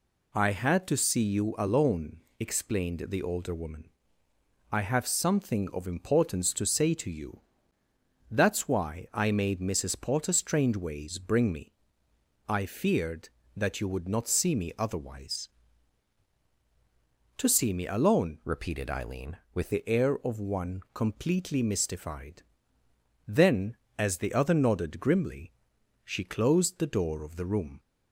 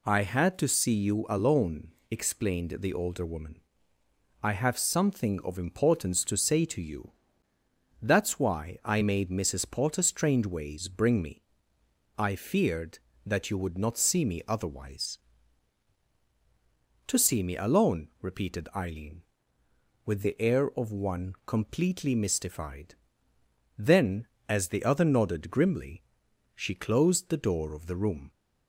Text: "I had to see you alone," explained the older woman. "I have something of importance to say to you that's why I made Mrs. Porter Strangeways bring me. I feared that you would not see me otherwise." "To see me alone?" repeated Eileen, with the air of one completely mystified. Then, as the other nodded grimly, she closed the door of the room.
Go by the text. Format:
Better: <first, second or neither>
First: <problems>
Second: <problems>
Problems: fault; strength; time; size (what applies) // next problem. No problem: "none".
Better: second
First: pauses between "you" and "that's"; noticeable; at 7.4 s; 0.90 s long // changes voice from "repeated" to "with"; from 18.4 to 19.7 s; 1.3 s long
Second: pauses between "you" and "that's"; noticeable; at 7.1 s; 0.90 s long